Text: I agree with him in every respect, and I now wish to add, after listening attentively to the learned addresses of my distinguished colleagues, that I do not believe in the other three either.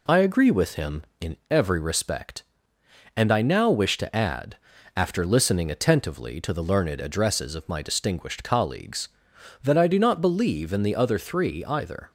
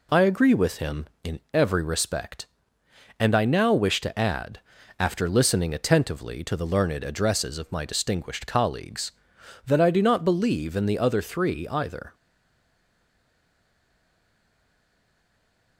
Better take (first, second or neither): first